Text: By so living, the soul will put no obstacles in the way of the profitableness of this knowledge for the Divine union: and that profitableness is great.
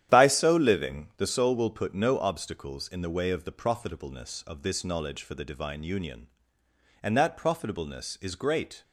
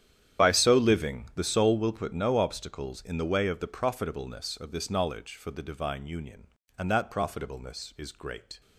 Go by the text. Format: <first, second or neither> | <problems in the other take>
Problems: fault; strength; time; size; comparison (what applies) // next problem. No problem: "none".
first | loses the start of "By"; at 0.3 s; 25 ms // starts louder than the rest; strong; until 1.5 s; 10.5 dB; strong in the first